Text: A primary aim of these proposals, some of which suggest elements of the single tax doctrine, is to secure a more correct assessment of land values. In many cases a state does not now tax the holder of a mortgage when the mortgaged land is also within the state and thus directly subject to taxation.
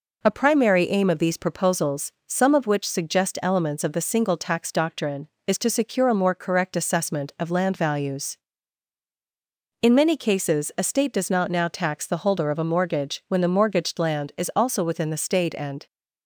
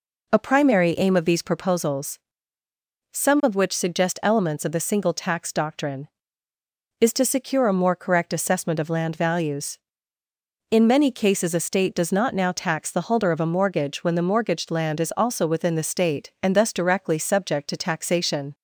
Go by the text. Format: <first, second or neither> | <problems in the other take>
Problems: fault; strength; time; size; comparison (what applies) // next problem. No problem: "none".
second | stops before "thus directly subject to taxation"; at 15.8 s